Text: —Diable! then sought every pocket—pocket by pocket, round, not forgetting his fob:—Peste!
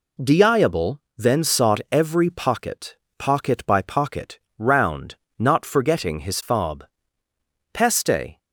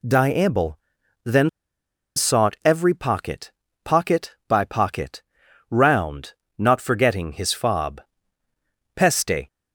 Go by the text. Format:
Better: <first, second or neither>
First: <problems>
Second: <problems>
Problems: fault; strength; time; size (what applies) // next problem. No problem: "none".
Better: first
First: none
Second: pauses between "then" and "sought"; noticeable; at 1.4 s; 0.67 s long